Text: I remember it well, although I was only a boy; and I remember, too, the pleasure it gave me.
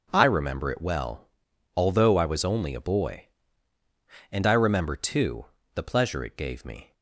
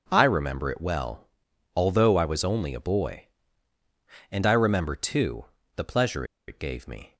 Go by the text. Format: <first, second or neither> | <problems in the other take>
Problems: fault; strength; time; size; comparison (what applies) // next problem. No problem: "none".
first | pauses between "pleasure" and "it"; slight; at 6.2 s; 0.23 s long